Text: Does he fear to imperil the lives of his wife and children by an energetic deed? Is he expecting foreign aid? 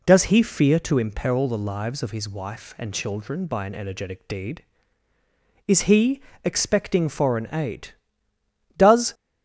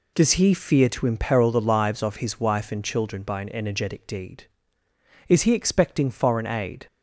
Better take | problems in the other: second | pauses between "he" and "expecting"; slight; at 6.1 s; 0.24 s long // goes on to say "Does"; slight; from 8.7 s on; 0.36 s long

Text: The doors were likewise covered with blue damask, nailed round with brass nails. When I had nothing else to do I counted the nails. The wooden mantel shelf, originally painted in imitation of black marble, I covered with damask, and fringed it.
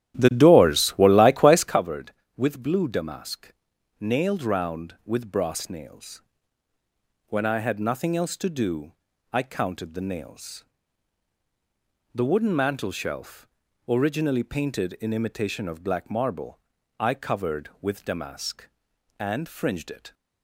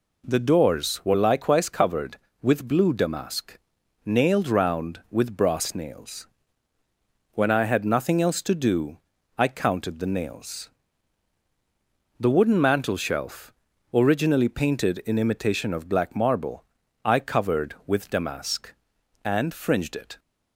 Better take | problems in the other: second | starts louder than the rest; strong; until 1.8 s; 12.5 dB // pauses between "do" and "I"; at 8.9 s; 0.38 s long; also in the second

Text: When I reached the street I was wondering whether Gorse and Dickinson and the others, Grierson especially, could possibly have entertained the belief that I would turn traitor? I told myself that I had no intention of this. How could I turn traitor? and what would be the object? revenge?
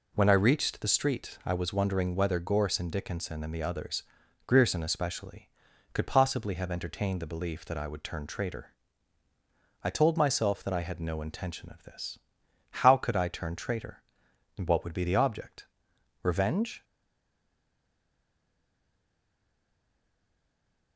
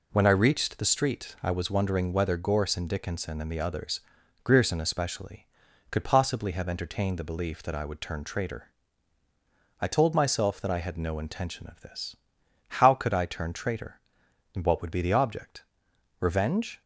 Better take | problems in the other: second | stays silent after the last word; strong; from 16.8 s on; 4.1 s long

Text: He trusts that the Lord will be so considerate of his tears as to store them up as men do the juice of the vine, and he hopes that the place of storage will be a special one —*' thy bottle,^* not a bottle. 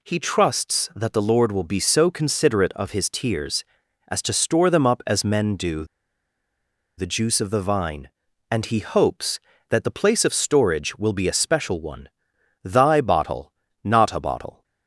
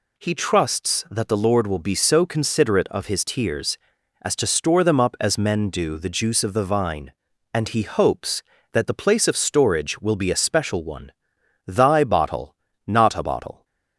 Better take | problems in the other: second | pauses between "do" and "the"; at 5.8 s; 1.1 s long

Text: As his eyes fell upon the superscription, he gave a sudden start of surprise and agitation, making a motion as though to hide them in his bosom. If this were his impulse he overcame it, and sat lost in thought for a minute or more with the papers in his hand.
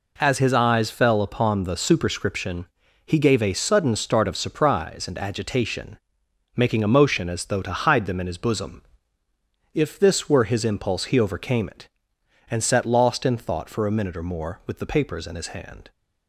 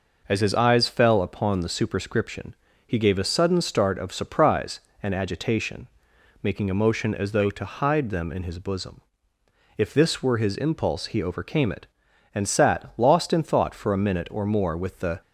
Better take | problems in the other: first | stops before "papers in his hand"; at 15.2 s

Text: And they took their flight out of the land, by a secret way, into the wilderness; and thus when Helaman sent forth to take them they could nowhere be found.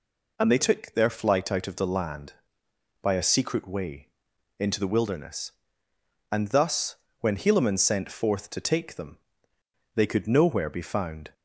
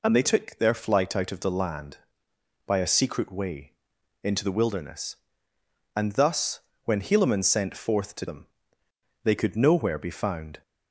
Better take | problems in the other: first | pauses between "thus" and "when"; slight; at 6.6 s; 0.24 s long; slight in the first // skips "take"; at 8.2 s // pauses between "them" and "they"; noticeable; at 8.4 s; 0.74 s long; noticeable in the first

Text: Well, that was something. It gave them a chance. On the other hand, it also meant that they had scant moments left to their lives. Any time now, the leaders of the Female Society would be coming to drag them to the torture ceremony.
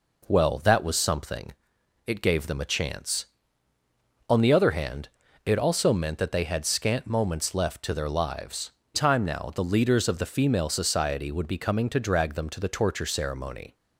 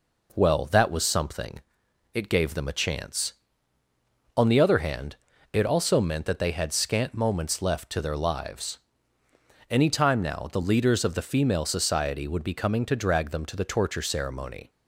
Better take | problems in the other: second | skips "Any"; at 8.8 s

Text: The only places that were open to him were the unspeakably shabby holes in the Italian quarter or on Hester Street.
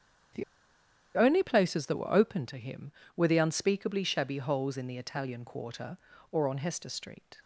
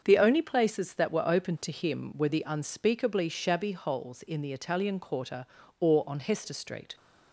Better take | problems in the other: second | starts louder than the rest; strong; until 2.0 s; 8.5 dB; also in the second // pauses between "The" and "only"; noticeable; at 0.4 s; 0.73 s long

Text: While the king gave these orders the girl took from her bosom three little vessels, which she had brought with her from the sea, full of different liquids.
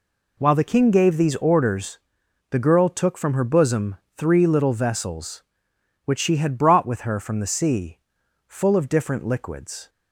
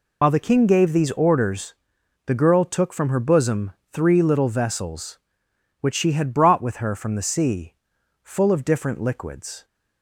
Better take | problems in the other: first | loses the start of "While"; at 0.2 s; 70 ms // pauses between "orders" and "the"; noticeable; at 1.7 s; 0.54 s long; noticeable in the first // pauses between "bosom" and "three"; slight; at 3.7 s; 0.20 s long; slight in the first

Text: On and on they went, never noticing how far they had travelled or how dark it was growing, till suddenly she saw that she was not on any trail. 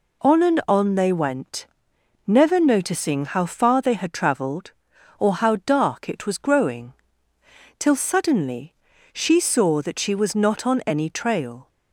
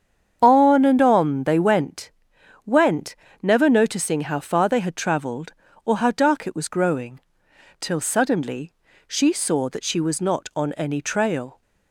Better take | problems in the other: first | starts louder than the rest; strong; until 1.4 s; 8 dB // says "went" twice; at 2.6 s // pauses between "suddenly" and "she"; slight; at 8.7 s; 0.34 s long; also in the first

